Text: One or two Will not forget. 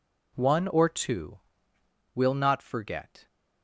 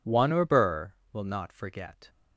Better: first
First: none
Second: says "burr" for "two"; at 0.4 s

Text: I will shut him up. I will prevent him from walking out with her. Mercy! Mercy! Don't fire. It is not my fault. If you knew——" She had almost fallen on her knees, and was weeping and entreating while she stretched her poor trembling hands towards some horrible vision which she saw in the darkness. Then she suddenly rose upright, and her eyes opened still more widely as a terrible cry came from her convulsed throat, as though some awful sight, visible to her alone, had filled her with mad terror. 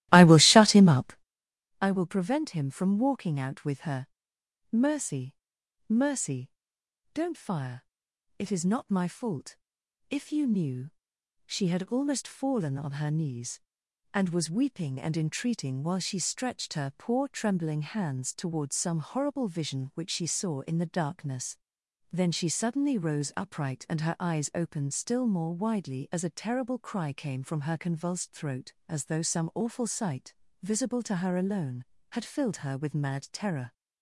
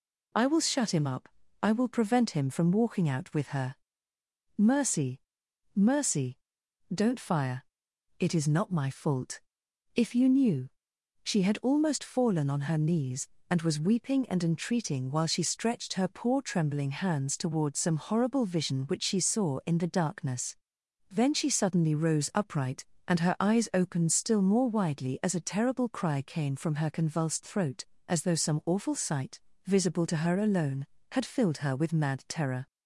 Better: second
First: starts louder than the rest; strong; until 1.3 s; 15.5 dB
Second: none

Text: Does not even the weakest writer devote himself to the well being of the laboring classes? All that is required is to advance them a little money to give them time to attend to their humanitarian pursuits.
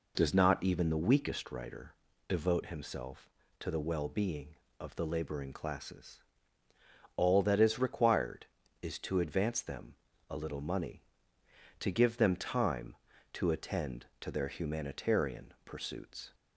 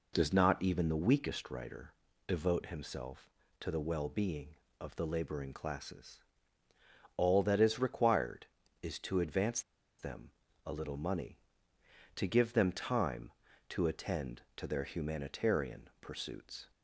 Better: first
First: pauses between "writer" and "devote"; slight; at 1.9 s; 0.36 s long // pauses between "them" and "a"; slight; at 9.9 s; 0.34 s long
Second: pauses between "writer" and "devote"; slight; at 1.9 s; 0.36 s long // pauses between "advance" and "them"; at 9.6 s; 0.38 s long // pauses between "them" and "a"; slight; at 10.3 s; 0.34 s long

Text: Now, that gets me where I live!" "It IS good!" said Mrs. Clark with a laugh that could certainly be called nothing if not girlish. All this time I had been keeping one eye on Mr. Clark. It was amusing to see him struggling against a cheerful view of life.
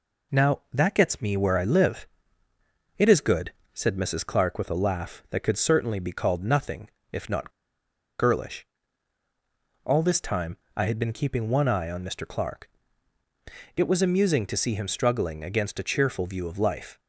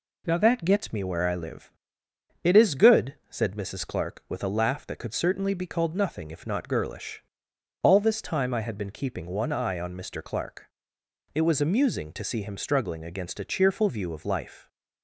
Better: second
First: pauses between "nothing" and "if"; slight; at 6.8 s; 0.22 s long // pauses between "not" and "girlish"; noticeable; at 7.5 s; 0.68 s long // pauses between "time" and "I"; slight; at 10.5 s; 0.20 s long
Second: none

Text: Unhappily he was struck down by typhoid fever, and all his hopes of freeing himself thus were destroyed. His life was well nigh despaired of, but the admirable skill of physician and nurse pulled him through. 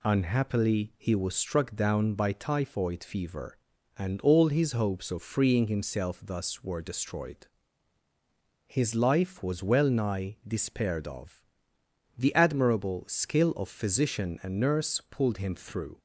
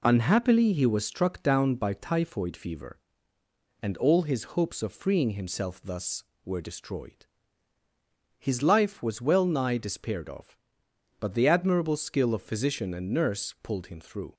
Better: second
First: skips "but"; at 11.7 s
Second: none

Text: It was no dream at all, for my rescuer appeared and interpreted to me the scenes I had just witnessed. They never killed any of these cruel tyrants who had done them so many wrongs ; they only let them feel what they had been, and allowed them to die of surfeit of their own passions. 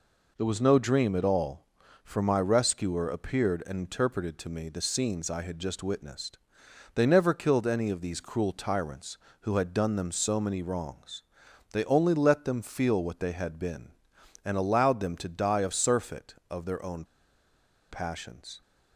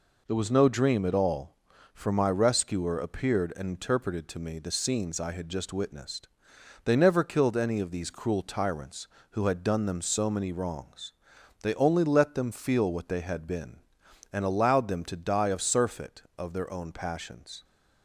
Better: second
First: pauses between "own" and "passions"; noticeable; at 17.0 s; 0.87 s long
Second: none

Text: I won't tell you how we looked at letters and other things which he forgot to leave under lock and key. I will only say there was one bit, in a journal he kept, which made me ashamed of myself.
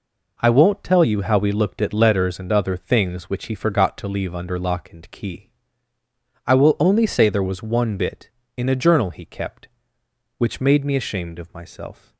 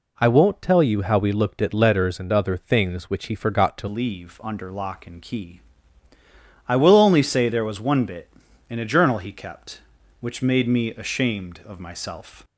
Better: first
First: none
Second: changes voice at "leave"; from 3.8 s on; 8.6 s long

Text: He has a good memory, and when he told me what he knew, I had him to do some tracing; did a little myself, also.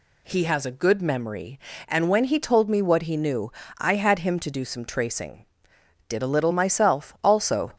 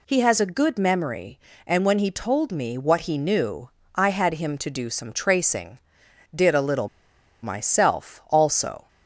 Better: first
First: none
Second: pauses between "little" and "myself"; noticeable; at 6.8 s; 0.55 s long

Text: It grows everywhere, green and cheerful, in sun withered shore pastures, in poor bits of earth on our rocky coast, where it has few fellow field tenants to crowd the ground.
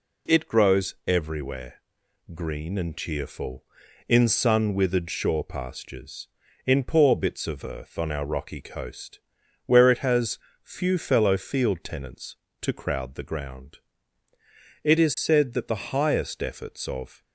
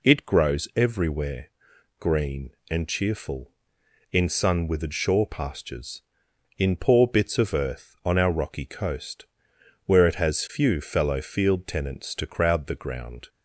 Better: second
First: pauses between "has" and "few"; slight; at 10.3 s; 0.26 s long // goes on to say "It is said that the highest efforts of"; strong; from 14.8 s on; 2.4 s long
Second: none

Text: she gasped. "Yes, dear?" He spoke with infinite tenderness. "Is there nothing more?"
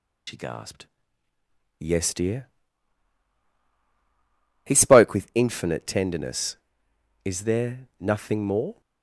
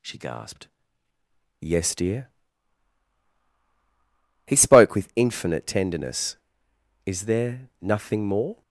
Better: second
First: loses the start of "she"; at 0.2 s; 75 ms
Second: none

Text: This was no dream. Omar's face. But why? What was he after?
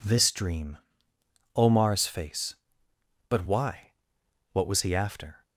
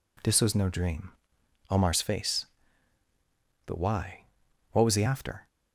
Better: second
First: skips "was no"; at 0.3 s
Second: none

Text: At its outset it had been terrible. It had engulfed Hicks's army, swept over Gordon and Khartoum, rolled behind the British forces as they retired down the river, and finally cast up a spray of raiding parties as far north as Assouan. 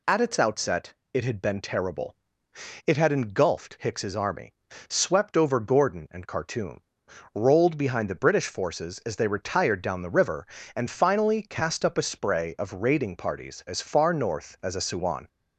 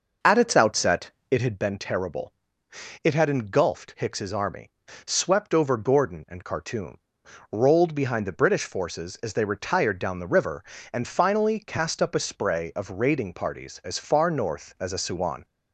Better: first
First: pauses between "outset" and "it"; slight; at 0.9 s; 0.22 s long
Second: starts louder than the rest; noticeable; until 1.6 s; 6 dB // pauses between "outset" and "it"; slight; at 1.0 s; 0.22 s long

